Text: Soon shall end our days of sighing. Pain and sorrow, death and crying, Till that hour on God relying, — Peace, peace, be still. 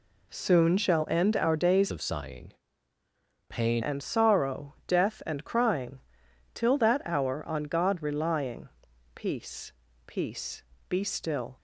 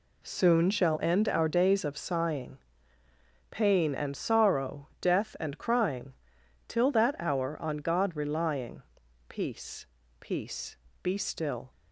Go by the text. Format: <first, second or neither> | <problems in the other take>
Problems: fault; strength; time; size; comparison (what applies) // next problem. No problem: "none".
second | changes voice from "of" to "Pain"; from 1.9 to 3.8 s; 1.9 s long